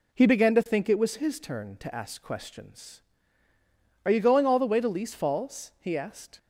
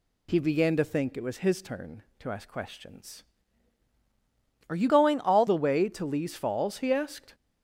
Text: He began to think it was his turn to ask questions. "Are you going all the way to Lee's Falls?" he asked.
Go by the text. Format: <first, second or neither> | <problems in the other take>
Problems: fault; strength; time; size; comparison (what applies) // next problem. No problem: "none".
first | changes voice from "going" to "all"; from 4.8 to 5.4 s; 0.6 s long